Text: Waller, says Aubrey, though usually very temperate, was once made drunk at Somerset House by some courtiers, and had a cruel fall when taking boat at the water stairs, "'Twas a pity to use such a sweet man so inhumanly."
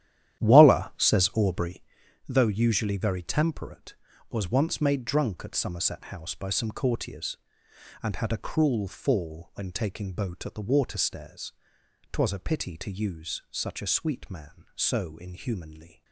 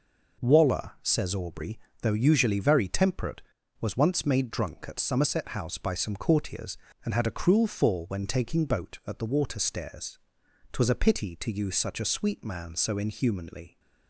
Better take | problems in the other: second | starts louder than the rest; strong; until 1.9 s; 11.5 dB

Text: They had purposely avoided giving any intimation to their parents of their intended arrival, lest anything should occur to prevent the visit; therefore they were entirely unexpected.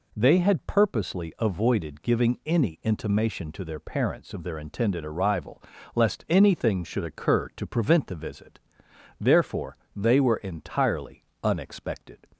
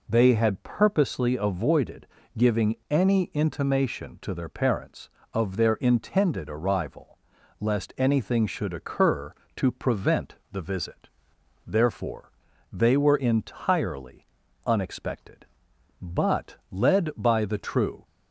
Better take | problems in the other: first | pauses between "avoided" and "giving"; slight; at 2.0 s; 0.30 s long // pauses between "giving" and "any"; slight; at 2.7 s; 0.16 s long // pauses between "prevent" and "the"; slight; at 10.3 s; 0.16 s long // pauses between "therefore" and "they"; at 12.3 s; 0.40 s long; slight in the first // pauses between "entirely" and "unexpected"; at 14.2 s; 0.40 s long; slight in the first // goes on to say "But led by the true"; strong; from 16.0 s on; 2.0 s long

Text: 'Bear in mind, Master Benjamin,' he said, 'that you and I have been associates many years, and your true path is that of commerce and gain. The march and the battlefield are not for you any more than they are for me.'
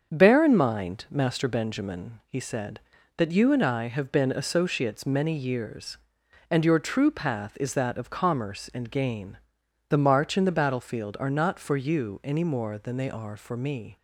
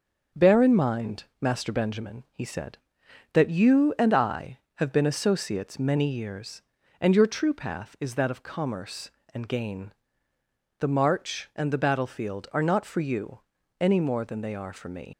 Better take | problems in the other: first | starts louder than the rest; until 1.5 s; 7 dB; also in the first // pauses between "you" and "any"; at 13.4 s; 0.38 s long // leaves "me" unfinished; at 15.1 s; 110 ms

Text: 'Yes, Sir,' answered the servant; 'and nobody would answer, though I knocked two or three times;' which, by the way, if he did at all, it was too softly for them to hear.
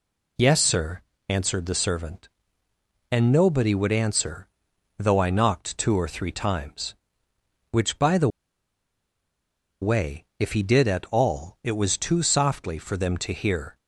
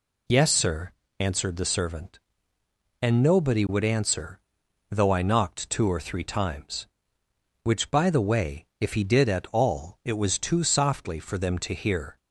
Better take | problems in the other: second | pauses between "the" and "way"; strong; at 8.2 s; 1.5 s long

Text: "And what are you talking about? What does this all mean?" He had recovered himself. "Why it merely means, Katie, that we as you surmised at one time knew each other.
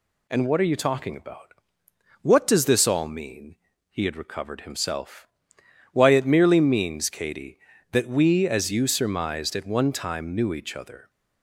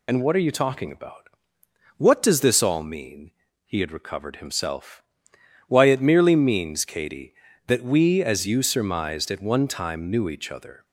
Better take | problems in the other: first | loses the start of "And"; at 0.0 s; 35 ms

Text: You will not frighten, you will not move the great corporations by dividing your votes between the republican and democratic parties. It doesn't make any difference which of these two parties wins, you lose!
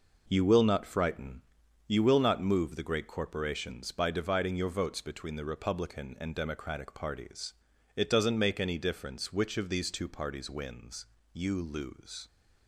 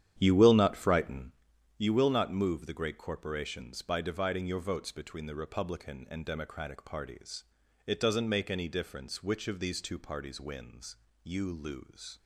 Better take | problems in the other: first | starts louder than the rest; strong; until 1.4 s; 10 dB

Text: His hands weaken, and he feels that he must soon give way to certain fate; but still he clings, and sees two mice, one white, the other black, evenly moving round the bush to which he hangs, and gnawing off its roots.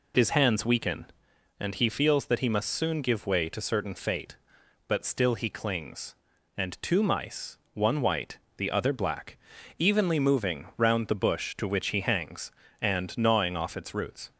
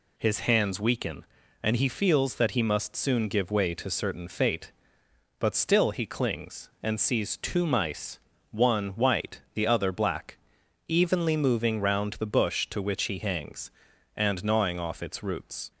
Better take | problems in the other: second | skips "sees"; at 6.8 s

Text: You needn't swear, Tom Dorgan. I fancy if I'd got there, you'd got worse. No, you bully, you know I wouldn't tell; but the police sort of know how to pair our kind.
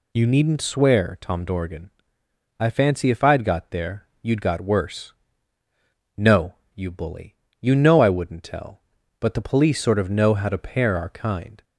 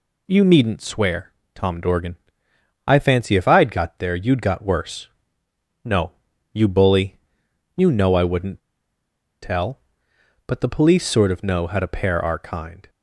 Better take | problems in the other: first | pauses between "wouldn't" and "tell"; noticeable; at 8.5 s; 0.84 s long

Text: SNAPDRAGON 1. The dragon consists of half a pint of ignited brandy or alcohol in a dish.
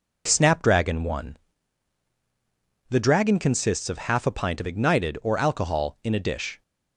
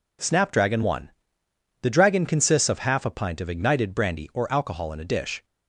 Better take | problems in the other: second | skips "brandy"; at 5.2 s

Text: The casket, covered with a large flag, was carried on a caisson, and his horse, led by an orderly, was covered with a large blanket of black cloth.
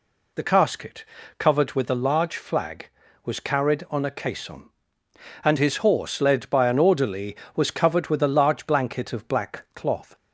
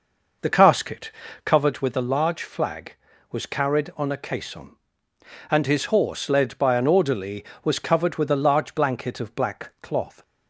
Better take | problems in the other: first | starts louder than the rest; noticeable; until 1.7 s; 5.5 dB

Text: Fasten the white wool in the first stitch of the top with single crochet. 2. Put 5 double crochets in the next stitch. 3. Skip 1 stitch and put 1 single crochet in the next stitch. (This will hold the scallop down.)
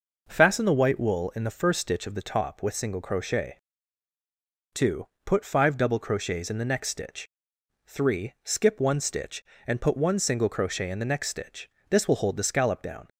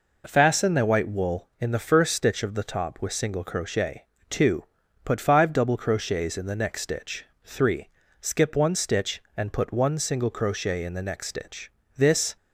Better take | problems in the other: first | stops before "will hold the scallop down"; at 12.3 s

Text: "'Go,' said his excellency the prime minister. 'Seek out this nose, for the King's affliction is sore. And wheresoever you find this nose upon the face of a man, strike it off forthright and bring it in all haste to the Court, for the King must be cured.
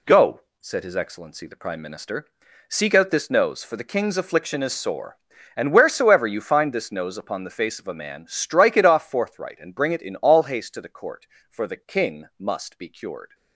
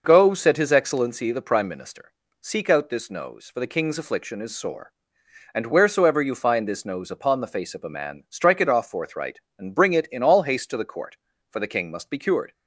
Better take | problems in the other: neither | none

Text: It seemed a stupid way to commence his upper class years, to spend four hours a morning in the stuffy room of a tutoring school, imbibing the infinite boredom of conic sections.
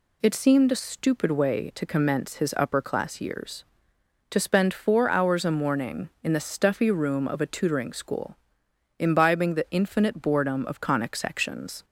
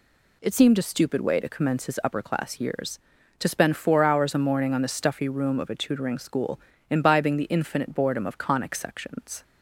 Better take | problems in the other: first | says "on" for "in"; at 4.7 s

